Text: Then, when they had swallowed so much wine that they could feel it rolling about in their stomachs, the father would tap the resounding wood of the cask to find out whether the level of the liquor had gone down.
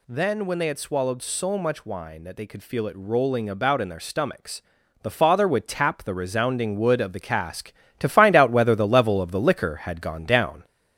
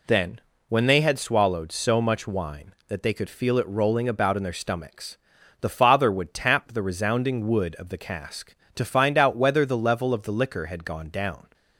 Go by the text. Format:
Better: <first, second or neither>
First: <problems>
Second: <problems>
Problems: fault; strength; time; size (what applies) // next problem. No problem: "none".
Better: second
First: gets louder; noticeable; throughout; 4.5 dB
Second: none